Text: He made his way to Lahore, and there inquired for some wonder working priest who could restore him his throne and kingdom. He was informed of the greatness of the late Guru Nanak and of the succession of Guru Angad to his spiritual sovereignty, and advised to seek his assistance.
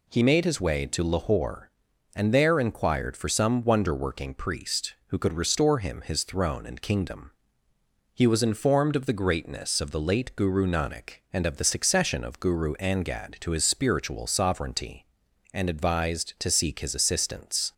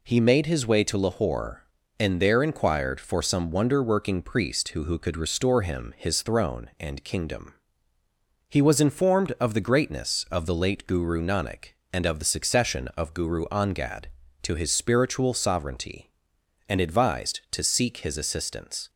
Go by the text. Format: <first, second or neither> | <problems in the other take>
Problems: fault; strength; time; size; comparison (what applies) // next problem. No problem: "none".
first | says "who" twice; at 4.8 s